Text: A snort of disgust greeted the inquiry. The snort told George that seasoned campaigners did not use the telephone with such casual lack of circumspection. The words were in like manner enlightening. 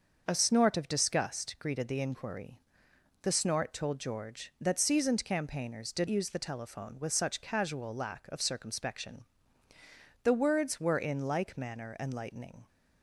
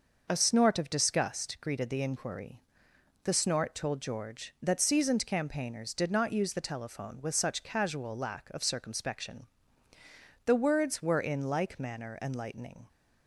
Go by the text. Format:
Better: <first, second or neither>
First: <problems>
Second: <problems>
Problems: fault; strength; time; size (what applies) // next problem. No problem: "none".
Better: second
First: starts louder than the rest; until 1.2 s; 6.5 dB // skips "not"; at 6.0 s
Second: none